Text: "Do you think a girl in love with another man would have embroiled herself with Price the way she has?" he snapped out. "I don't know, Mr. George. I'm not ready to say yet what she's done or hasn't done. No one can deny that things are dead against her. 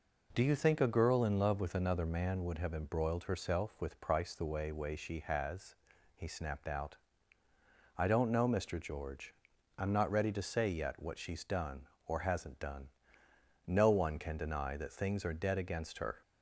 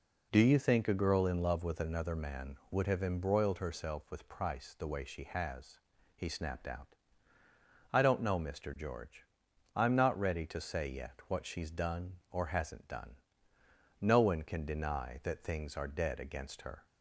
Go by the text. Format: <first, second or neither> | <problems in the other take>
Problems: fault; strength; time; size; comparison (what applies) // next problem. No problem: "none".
second | says "way" twice; at 4.7 s